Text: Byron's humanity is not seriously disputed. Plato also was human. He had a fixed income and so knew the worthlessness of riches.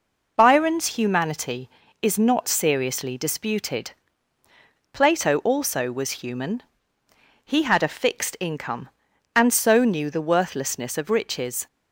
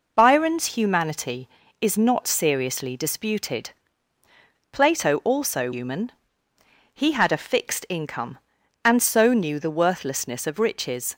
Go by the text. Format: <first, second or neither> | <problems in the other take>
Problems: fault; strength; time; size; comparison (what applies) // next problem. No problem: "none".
first | skips "was"; at 5.7 s